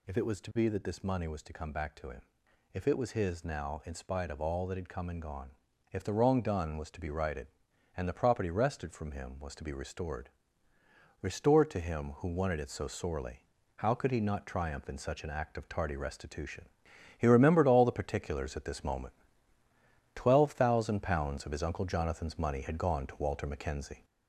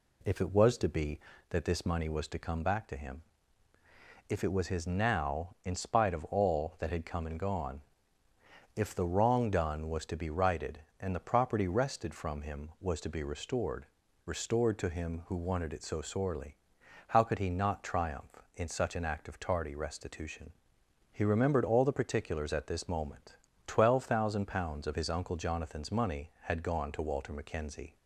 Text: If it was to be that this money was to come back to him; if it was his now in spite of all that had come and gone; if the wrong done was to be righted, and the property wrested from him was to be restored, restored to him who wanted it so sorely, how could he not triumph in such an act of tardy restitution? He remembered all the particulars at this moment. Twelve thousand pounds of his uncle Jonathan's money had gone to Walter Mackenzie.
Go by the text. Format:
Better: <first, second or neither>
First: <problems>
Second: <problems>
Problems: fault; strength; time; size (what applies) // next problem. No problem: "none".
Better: second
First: gets louder; throughout; 3.5 dB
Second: none